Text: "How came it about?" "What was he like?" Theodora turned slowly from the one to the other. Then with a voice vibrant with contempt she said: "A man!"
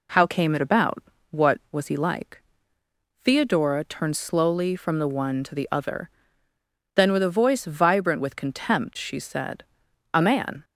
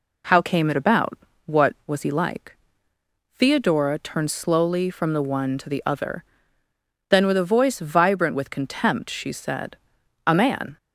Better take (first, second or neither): neither